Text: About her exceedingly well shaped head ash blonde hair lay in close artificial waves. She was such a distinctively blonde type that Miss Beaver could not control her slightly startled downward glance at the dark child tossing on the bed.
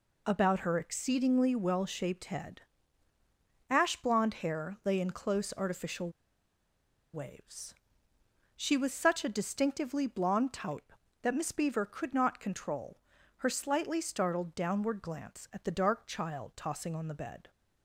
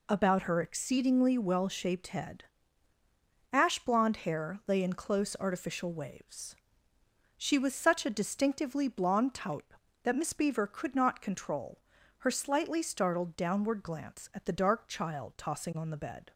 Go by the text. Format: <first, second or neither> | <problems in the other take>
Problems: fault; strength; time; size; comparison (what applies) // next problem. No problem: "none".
second | pauses between "head" and "ash"; at 2.6 s; 1.1 s long; also in the second // pauses between "artificial" and "waves"; at 6.1 s; 1.0 s long // pauses between "control" and "her"; at 12.9 s; 0.38 s long; also in the second